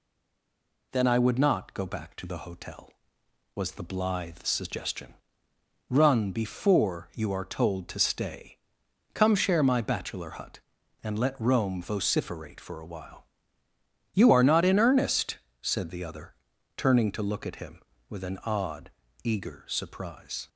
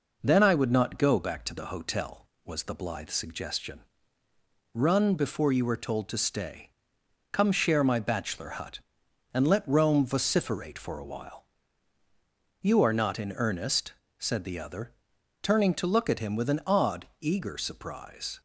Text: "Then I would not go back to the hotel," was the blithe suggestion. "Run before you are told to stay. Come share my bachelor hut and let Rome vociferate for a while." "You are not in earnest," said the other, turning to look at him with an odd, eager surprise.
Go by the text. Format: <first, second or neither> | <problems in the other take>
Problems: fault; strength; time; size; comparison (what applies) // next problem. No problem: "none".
second | stays silent before the first word; slight; until 0.9 s; 0.9 s long